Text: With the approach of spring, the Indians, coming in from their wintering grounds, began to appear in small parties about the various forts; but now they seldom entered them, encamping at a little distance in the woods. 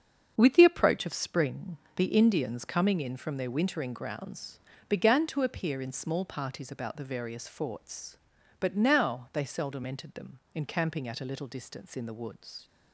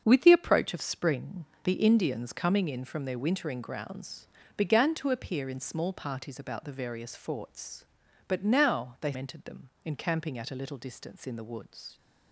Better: first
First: starts louder than the rest; until 1.3 s; 7 dB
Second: starts louder than the rest; until 1.0 s; 7 dB // skips "seldom"; at 9.1 s

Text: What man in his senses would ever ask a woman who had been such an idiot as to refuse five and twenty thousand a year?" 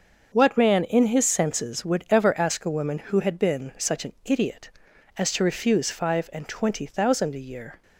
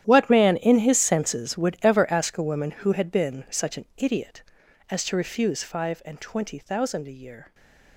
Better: first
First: starts louder than the rest; until 1.3 s; 6.5 dB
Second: gets quieter; strong; throughout; 17 dB // starts louder than the rest; strong; until 1.0 s; 11 dB // stays silent after the last word; slight; from 7.4 s on; 0.5 s long

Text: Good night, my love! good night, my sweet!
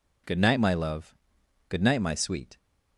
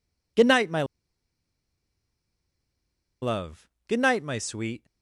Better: first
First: none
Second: pauses between "my" and "love"; strong; at 0.8 s; 2.3 s long

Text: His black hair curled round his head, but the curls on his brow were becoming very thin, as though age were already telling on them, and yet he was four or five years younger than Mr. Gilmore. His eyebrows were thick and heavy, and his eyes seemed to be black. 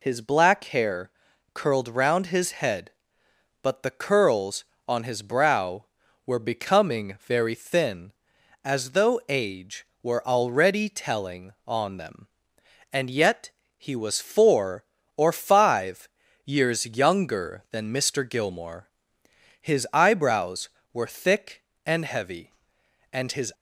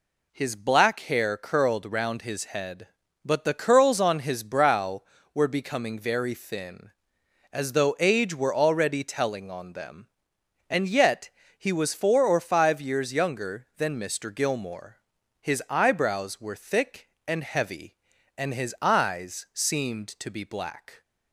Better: second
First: pauses between "hair" and "curled"; at 1.1 s; 0.44 s long // pauses between "yet" and "he"; slight; at 13.5 s; 0.28 s long // pauses between "five" and "years"; slight; at 16.0 s; 0.36 s long // stops before "eyes seemed to be black"; at 23.5 s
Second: pauses between "yet" and "he"; slight; at 11.2 s; 0.28 s long

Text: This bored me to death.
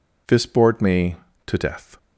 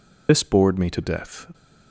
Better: first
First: none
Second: loses the start of "This"; at 0.2 s; 125 ms

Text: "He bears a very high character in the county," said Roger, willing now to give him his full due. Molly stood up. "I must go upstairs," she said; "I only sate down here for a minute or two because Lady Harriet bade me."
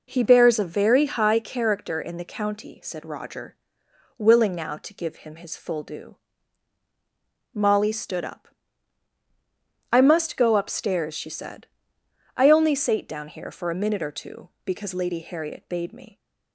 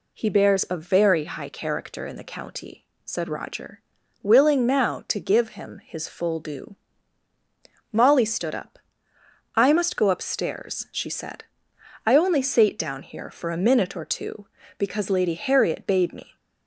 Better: neither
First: none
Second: none

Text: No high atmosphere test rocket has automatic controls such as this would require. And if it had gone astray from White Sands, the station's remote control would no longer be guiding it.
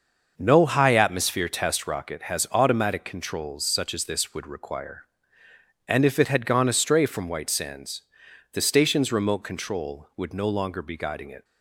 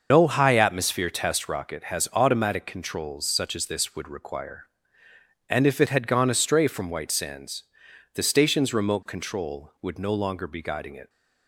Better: first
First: starts louder than the rest; noticeable; until 1.3 s; 6 dB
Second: loses the start of "No"; at 0.1 s; 110 ms // starts louder than the rest; noticeable; until 1.1 s; 6 dB

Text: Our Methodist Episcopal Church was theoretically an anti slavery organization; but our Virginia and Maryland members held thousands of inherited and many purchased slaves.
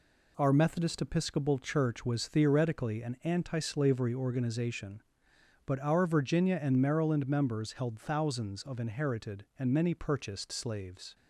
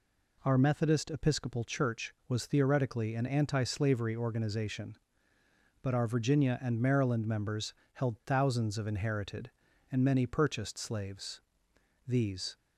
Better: first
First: none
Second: pauses between "members" and "held"; slight; at 7.7 s; 0.18 s long // goes on to say "These"; slight; from 12.0 s on; 0.48 s long

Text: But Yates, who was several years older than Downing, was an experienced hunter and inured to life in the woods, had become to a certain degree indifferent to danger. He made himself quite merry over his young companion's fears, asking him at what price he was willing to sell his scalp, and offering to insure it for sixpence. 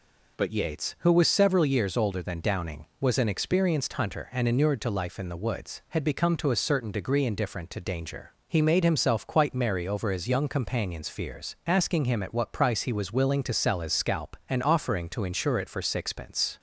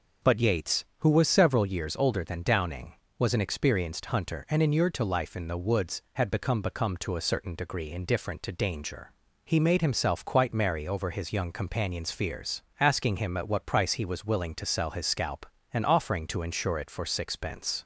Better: first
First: none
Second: says "become" twice; at 6.6 s

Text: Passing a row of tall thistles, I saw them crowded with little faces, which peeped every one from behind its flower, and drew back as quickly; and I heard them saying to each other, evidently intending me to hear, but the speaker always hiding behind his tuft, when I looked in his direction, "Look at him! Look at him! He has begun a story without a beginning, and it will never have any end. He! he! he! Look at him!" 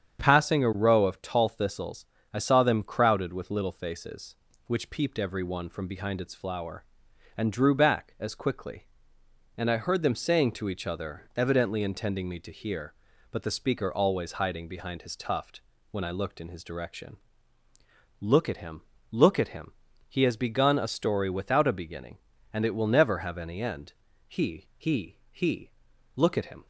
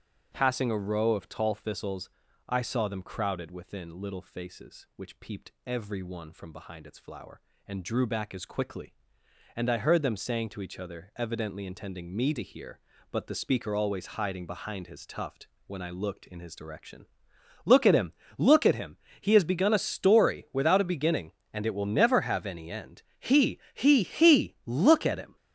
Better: first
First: starts louder than the rest; strong; until 1.2 s; 8.5 dB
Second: starts louder than the rest; strong; until 1.3 s; 8.5 dB // says "within" for "with"; at 3.5 s

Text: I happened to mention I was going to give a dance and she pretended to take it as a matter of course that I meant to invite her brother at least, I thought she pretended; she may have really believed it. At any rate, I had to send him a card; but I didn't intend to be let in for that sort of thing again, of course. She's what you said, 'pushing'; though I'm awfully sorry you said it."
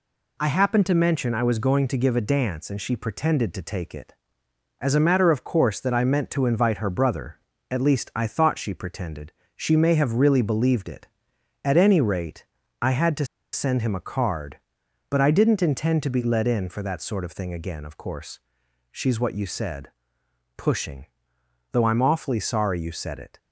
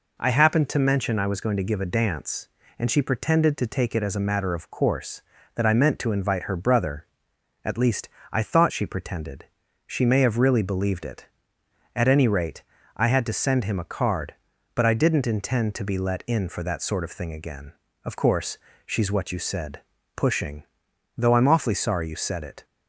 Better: second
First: pauses between "to" and "send"; slight; at 13.2 s; 0.27 s long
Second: none

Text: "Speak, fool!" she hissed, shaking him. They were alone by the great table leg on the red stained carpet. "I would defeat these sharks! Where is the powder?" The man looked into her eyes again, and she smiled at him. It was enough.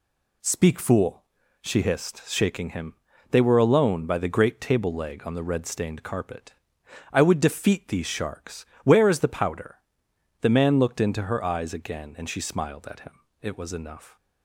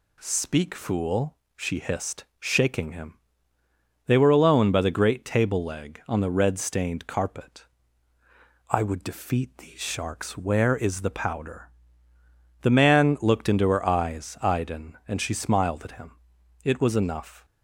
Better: first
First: none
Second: says "iden" for "again"; at 14.4 s

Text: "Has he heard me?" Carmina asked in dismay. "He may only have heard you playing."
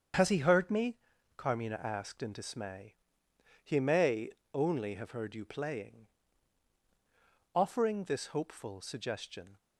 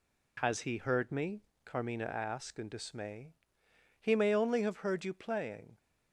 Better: second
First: starts louder than the rest; strong; until 1.5 s; 7.5 dB // pauses between "may" and "only"; slight; at 4.3 s; 0.22 s long // goes on to say "Offering this hopeful suggestion"; strong; from 7.5 s on; 2.0 s long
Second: none

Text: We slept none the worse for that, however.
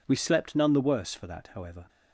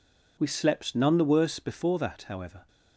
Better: first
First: none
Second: says "before" for "for"; at 1.5 s

